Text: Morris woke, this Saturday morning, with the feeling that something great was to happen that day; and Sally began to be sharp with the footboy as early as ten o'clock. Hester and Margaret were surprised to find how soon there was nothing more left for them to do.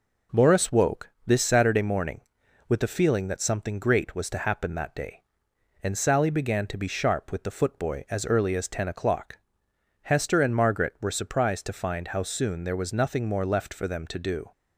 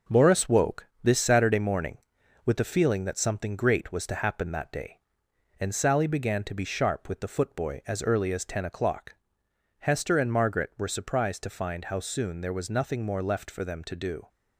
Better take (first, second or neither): first